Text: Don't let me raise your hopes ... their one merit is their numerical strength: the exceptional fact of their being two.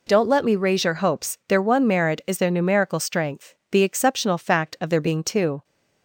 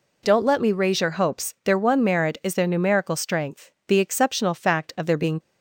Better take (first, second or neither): first